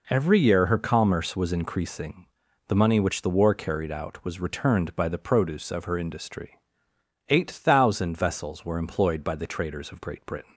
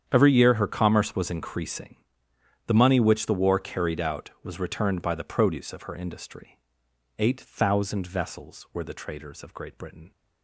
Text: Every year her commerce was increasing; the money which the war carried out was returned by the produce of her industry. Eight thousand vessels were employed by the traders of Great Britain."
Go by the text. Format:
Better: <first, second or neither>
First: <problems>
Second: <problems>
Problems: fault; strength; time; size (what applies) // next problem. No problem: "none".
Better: first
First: none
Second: starts louder than the rest; strong; until 1.0 s; 8.5 dB // skips "employed by"; at 8.8 s